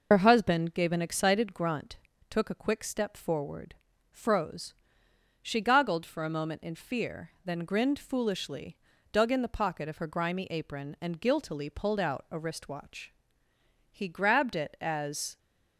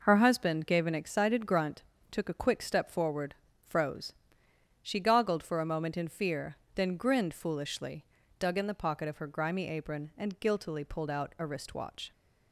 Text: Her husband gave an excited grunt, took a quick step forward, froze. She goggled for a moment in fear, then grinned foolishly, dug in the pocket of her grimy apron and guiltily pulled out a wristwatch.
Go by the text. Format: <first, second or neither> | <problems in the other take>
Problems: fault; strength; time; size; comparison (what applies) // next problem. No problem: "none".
second | goes on to say "He grabbed it as"; from 13.8 s on; 1.4 s long